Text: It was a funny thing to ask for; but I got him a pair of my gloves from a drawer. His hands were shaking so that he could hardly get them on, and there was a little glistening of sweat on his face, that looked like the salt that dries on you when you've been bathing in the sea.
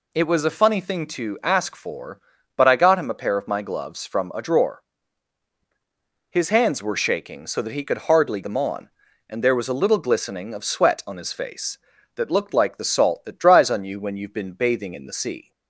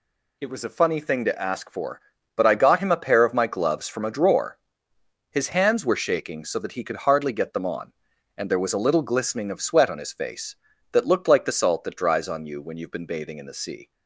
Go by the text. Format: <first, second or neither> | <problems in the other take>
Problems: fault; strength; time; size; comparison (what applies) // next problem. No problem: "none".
second | skips "get"; at 8.4 s